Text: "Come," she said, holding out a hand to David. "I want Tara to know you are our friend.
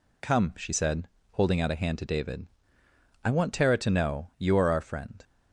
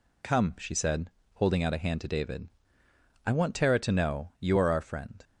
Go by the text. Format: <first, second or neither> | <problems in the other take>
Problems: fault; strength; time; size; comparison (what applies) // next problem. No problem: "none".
neither | none